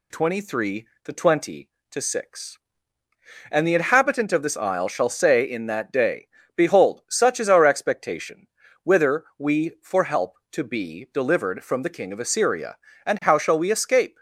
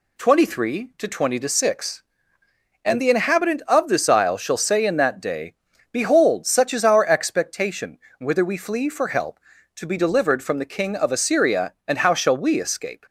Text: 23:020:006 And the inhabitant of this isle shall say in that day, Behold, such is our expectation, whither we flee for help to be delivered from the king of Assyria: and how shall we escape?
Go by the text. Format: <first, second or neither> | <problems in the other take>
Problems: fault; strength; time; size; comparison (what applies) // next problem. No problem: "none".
second | skips "flee"; at 9.7 s